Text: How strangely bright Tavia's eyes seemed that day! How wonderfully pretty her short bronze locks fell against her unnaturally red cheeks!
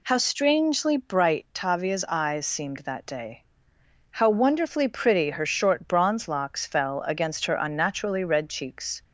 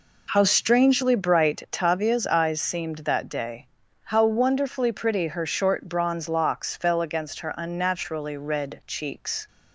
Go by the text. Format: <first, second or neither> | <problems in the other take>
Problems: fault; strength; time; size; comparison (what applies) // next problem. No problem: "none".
neither | none